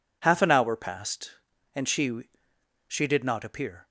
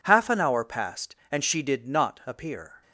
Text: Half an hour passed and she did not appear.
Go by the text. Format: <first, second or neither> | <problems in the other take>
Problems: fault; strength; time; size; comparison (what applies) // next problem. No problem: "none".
second | says "she" twice; at 2.8 s